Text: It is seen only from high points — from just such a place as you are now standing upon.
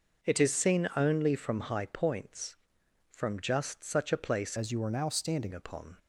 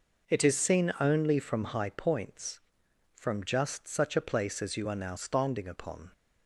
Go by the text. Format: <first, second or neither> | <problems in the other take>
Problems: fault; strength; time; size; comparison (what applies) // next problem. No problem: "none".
second | changes voice from "as" to "standing"; from 4.5 to 5.5 s; 1.0 s long